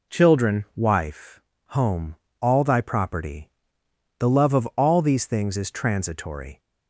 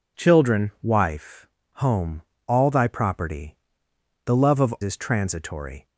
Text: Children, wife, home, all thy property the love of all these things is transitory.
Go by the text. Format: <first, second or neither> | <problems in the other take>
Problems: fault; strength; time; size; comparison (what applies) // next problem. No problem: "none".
first | pauses between "property" and "the"; noticeable; at 3.5 s; 0.70 s long; noticeable in the first // skips "all these things"; at 4.7 s